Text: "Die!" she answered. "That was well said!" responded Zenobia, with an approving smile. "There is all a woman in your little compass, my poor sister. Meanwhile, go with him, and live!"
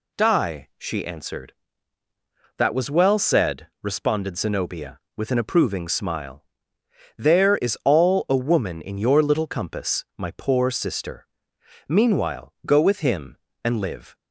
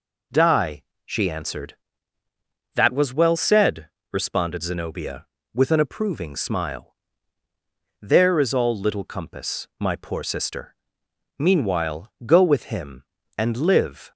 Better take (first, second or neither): first